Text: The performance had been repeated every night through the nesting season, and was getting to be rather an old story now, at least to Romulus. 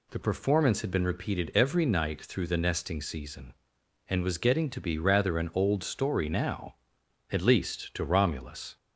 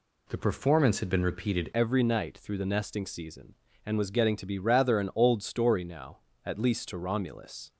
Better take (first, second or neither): first